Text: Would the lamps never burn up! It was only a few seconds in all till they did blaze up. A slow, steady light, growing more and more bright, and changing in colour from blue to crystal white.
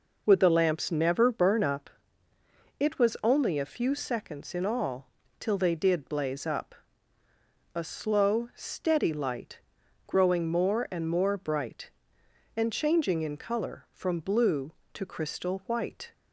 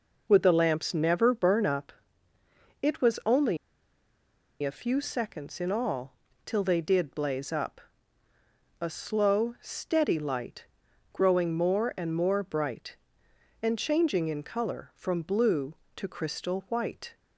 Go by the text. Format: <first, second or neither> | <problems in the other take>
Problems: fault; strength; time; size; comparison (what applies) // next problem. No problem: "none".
first | pauses between "only" and "a"; at 3.5 s; 1.0 s long // pauses between "all" and "till"; slight; at 6.1 s; 0.32 s long; slight in the first